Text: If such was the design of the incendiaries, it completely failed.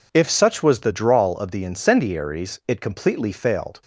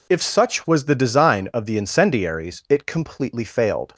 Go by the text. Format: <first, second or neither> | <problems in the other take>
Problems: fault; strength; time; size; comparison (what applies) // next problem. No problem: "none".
second | says "drawl" for "design"; at 0.9 s